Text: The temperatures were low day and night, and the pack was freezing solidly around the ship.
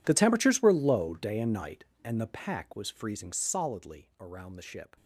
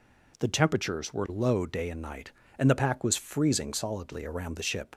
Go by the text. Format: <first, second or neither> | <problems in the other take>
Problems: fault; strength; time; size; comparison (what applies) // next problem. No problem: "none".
second | gets quieter; strong; throughout; 20.5 dB